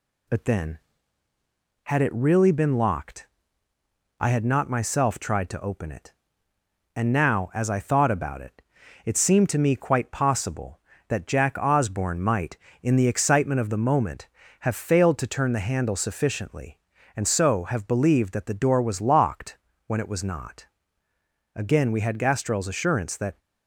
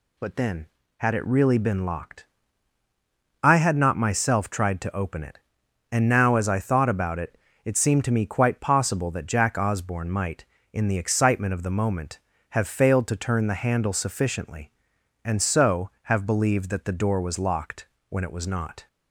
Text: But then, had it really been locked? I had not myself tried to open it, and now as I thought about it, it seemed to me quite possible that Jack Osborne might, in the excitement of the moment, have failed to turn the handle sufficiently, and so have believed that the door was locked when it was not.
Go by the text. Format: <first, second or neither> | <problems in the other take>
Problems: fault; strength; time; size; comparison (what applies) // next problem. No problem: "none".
second | pauses between "locked" and "when"; slight; at 19.5 s; 0.30 s long; slight in the second // goes on to say "Again we had Gastrell's assurance that"; strong; from 21.5 s on; 1.8 s long